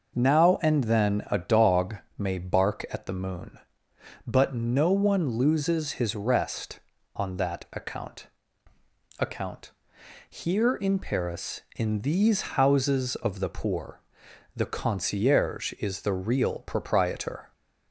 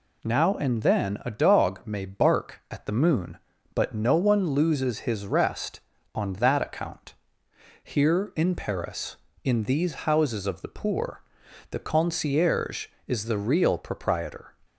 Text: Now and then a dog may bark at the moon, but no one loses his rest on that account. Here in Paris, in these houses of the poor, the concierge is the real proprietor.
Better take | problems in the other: second | pauses between "dog" and "may"; slight; at 1.9 s; 0.20 s long // says "account" twice; at 9.2 s

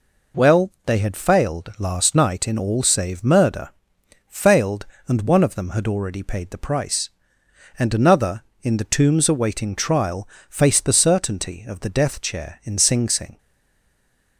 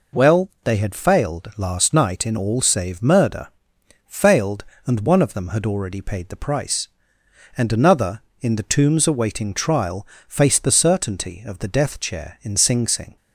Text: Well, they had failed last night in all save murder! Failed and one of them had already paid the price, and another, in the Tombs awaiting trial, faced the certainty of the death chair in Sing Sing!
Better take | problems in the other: second | stays silent after the last word; from 13.3 s on; 1.0 s long

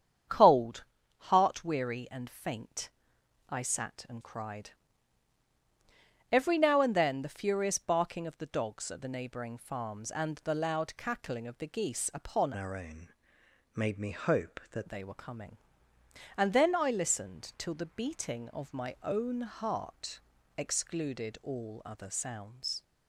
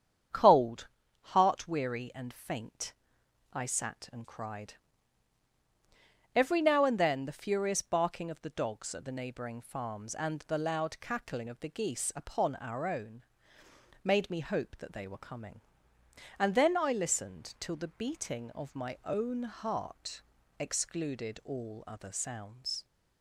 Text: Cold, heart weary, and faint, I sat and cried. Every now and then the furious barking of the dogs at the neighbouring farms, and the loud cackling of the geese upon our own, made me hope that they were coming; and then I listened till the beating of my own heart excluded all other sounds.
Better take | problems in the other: second | starts louder than the rest; strong; until 1.6 s; 8.5 dB; strong in the second // changes voice from "our" to "that"; from 12.5 to 14.8 s; 2.3 s long // pauses between "heart" and "excluded"; at 20.1 s; 0.38 s long; also in the second

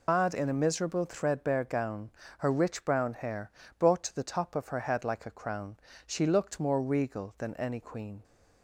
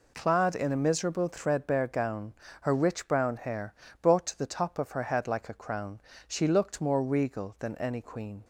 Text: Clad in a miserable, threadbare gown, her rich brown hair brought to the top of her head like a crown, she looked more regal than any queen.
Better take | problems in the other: second | loses the start of "Clad"; at 0.0 s; 135 ms // pauses between "hair" and "brought"; slight; at 3.5 s; 0.26 s long; slight in the second

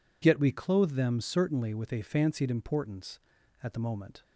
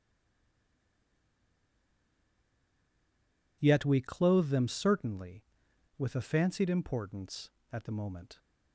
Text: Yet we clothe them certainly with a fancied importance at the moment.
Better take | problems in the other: first | stays silent before the first word; strong; until 3.6 s; 3.6 s long

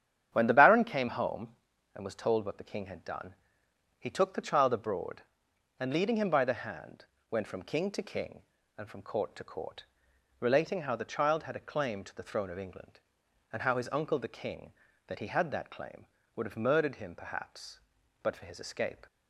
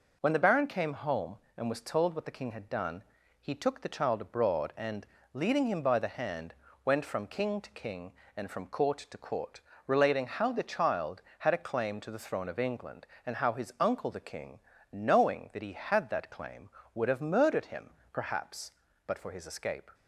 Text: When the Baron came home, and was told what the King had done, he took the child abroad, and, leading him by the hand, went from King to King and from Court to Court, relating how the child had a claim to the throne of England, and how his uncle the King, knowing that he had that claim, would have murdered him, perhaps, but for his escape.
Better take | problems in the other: second | starts louder than the rest; strong; until 1.3 s; 9.5 dB // skips "knowing"; at 14.8 s

